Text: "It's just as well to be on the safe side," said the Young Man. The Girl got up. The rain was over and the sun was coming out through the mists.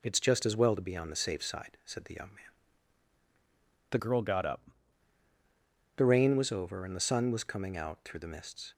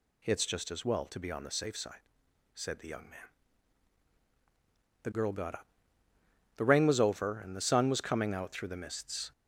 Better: second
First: changes voice from "Girl" to "up"; from 3.9 to 4.6 s; 0.7 s long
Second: none

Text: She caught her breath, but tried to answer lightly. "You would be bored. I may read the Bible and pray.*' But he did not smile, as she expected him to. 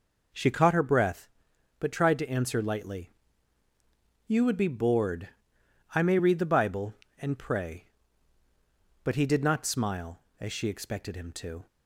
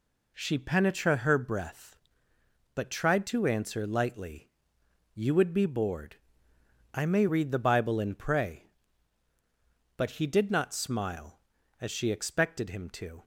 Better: first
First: none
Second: says "penetra" for "caught"; at 0.5 s

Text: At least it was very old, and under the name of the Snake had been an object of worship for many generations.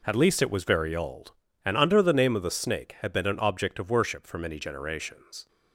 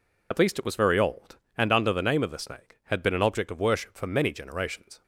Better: first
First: none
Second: loses the start of "At"; at 0.3 s; 50 ms

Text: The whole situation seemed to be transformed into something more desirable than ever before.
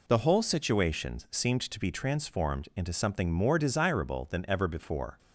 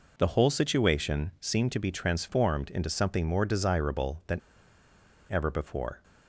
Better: first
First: none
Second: pauses between "than" and "ever"; noticeable; at 4.3 s; 0.94 s long

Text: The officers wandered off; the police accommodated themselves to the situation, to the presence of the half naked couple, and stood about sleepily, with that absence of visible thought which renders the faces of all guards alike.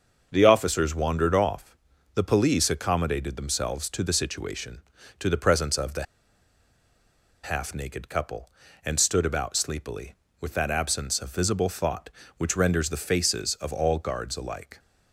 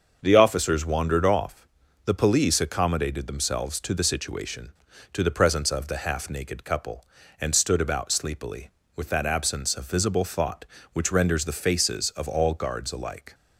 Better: second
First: starts louder than the rest; until 1.3 s; 6.5 dB // pauses between "the" and "half"; strong; at 6.0 s; 1.4 s long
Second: starts louder than the rest; until 1.2 s; 6.5 dB

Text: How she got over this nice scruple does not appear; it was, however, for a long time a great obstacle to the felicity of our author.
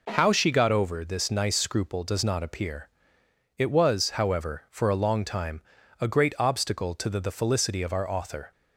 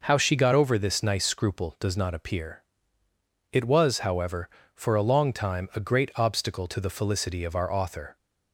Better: second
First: pauses between "time" and "a"; at 5.6 s; 0.38 s long // says "the" twice; at 7.1 s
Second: none

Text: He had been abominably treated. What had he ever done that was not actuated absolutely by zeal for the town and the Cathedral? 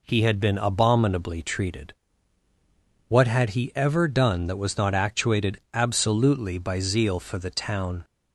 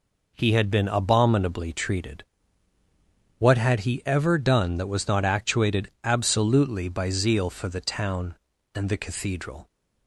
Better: second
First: stops before "and the Cathedral"; at 8.0 s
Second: none

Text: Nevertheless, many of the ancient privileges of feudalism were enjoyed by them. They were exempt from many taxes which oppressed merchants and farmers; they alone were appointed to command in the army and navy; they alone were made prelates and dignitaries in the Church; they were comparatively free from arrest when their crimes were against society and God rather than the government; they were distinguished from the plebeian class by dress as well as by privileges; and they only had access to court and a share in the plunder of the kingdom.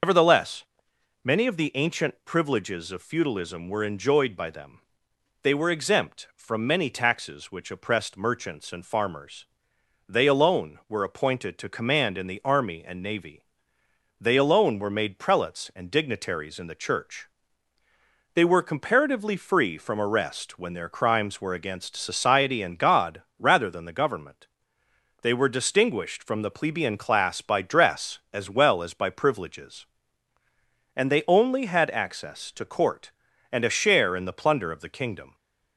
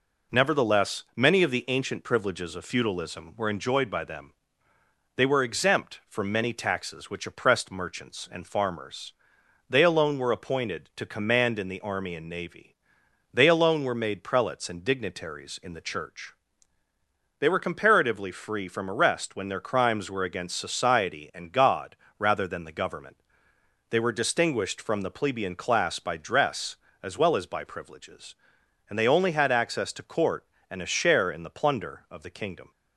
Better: second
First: loses the start of "Nevertheless"; at 0.0 s; 120 ms // starts louder than the rest; noticeable; until 1.6 s; 6 dB // pauses between "God" and "rather"; slight; at 23.2 s; 0.16 s long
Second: pauses between "God" and "rather"; slight; at 21.9 s; 0.22 s long

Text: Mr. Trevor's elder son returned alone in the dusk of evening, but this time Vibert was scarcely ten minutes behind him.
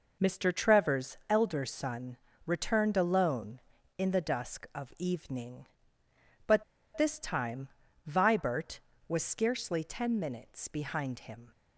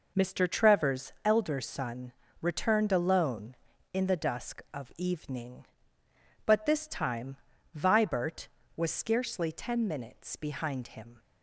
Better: second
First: pauses between "son" and "returned"; slight; at 2.1 s; 0.28 s long // pauses between "but" and "this"; slight; at 6.6 s; 0.33 s long // pauses between "time" and "Vibert"; at 7.6 s; 0.40 s long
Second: pauses between "son" and "returned"; slight; at 2.1 s; 0.28 s long // pauses between "time" and "Vibert"; at 7.3 s; 0.40 s long

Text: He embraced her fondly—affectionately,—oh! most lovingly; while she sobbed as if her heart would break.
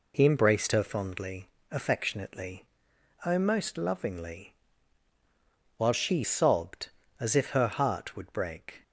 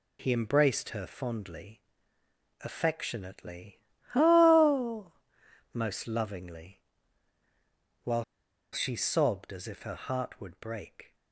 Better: first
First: none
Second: pauses between "while" and "she"; noticeable; at 8.2 s; 0.48 s long

